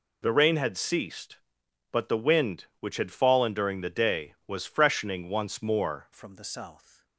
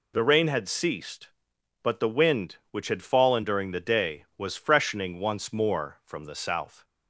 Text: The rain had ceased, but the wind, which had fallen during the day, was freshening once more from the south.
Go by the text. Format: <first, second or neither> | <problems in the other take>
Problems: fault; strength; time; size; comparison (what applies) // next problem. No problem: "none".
second | changes voice at "from"; from 6.1 s on; 0.9 s long